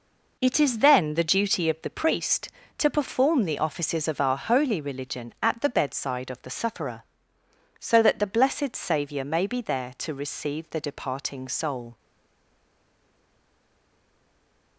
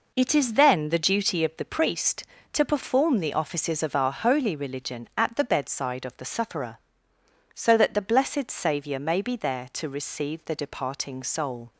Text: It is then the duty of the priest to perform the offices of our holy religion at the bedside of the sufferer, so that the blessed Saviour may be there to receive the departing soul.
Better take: second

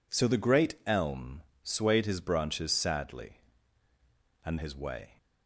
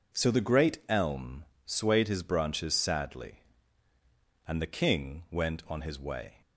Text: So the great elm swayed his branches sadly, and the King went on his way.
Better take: second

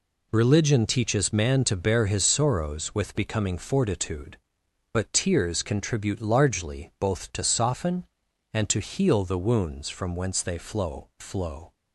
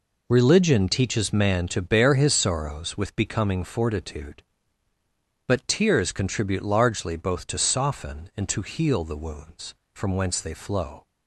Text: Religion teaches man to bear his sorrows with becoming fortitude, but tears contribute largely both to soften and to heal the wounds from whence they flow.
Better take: second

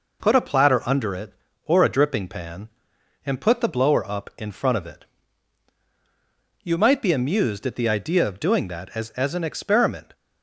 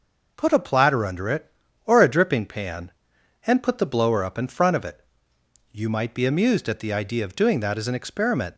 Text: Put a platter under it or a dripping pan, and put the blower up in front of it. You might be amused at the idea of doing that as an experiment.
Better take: second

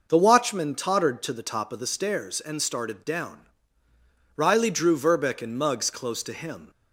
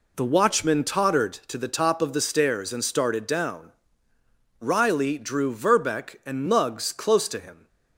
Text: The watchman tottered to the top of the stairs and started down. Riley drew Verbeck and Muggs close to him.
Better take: neither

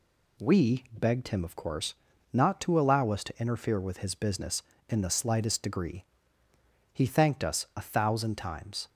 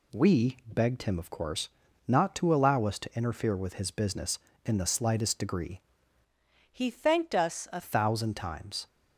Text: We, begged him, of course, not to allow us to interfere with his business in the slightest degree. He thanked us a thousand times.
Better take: first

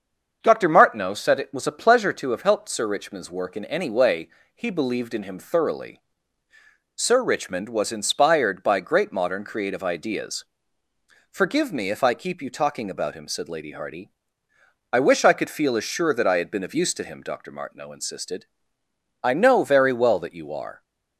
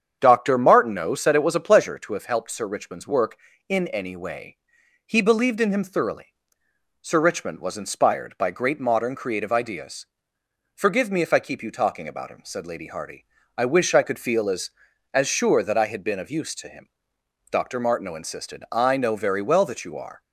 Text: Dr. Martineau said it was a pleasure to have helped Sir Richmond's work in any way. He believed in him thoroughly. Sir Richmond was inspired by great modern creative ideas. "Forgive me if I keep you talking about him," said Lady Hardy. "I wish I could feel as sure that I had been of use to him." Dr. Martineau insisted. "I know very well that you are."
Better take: first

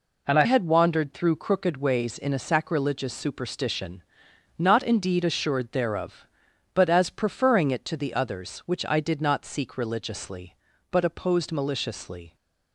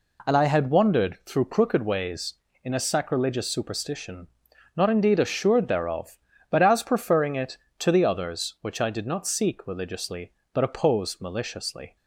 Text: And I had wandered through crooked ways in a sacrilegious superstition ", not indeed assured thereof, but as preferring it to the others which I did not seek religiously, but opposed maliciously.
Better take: second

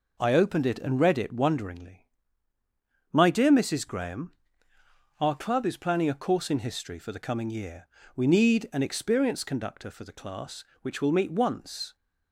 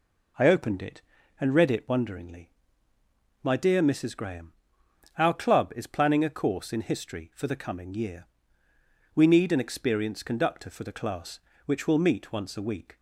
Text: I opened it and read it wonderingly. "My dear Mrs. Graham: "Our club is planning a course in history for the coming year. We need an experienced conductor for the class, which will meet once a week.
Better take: second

